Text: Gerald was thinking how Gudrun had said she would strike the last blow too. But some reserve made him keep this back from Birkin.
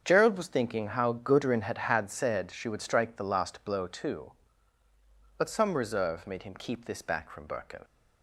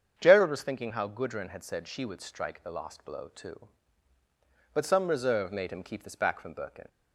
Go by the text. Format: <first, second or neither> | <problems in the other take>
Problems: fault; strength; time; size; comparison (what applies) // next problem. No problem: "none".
second | starts louder than the rest; strong; until 1.0 s; 7.5 dB; strong in the second // says "had" twice; at 1.7 s